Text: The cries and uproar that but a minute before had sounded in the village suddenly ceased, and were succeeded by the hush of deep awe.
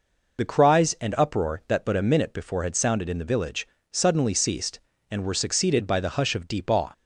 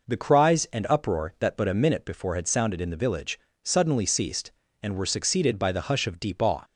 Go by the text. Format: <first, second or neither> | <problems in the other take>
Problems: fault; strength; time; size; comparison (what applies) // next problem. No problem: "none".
second | loses the start of "The"; at 0.3 s; 40 ms // pauses between "village" and "suddenly"; slight; at 3.6 s; 0.24 s long; slight in the second